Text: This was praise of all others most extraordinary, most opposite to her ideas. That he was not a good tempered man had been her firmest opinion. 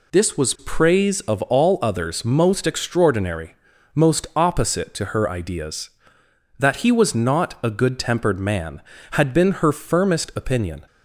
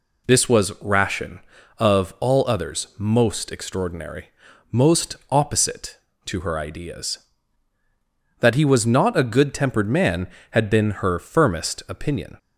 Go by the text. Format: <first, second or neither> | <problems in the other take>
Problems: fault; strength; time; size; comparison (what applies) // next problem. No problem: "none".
first | says "ration" for "praise"; at 0.8 s